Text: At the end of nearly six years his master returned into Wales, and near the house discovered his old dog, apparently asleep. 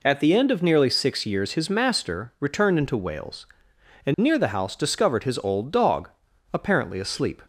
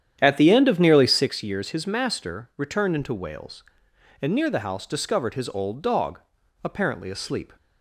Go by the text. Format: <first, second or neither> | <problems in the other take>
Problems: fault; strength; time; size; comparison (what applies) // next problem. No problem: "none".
first | starts louder than the rest; strong; until 1.3 s; 9.5 dB